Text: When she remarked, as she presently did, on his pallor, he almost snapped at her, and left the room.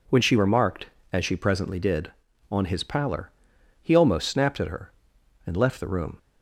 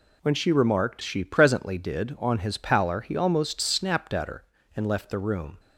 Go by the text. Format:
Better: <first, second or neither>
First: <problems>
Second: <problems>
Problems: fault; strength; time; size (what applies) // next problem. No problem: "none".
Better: first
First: none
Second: skips "as"; at 1.0 s